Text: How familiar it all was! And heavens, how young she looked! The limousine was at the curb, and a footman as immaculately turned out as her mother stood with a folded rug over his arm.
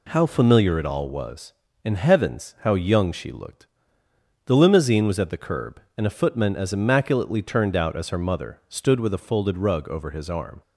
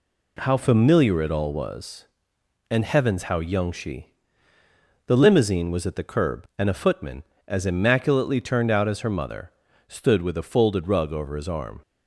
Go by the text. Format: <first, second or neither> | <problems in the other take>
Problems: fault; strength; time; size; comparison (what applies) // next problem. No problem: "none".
first | skips "looked"; at 4.5 s // pauses between "mother" and "stood"; at 9.4 s; 0.38 s long